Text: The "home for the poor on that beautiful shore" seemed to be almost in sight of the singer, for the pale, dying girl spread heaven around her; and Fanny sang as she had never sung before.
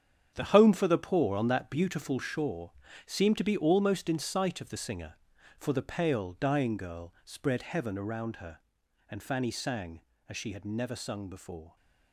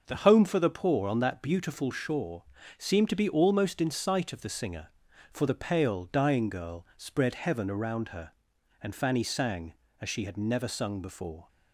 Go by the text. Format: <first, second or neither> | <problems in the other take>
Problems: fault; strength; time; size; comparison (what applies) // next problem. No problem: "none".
second | gets quieter; strong; throughout; 10.5 dB // starts louder than the rest; strong; until 1.3 s; 8 dB; noticeable in the second // pauses between "shore" and "seemed"; slight; at 2.7 s; 0.34 s long; slight in the second